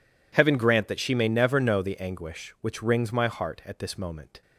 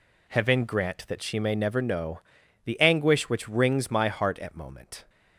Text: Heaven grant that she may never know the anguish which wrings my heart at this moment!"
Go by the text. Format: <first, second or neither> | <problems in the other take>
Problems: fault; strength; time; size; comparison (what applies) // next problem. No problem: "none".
first | pauses between "know" and "the"; noticeable; at 2.1 s; 0.46 s long // skips "this"; at 4.5 s